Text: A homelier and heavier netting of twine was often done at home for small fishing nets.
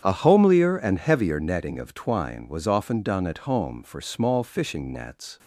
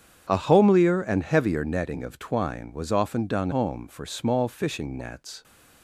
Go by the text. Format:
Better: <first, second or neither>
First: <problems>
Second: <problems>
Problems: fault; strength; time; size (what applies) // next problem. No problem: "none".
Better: first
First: starts louder than the rest; strong; until 1.0 s; 8.5 dB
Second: starts louder than the rest; strong; until 1.3 s; 8 dB // skips "at"; at 3.5 s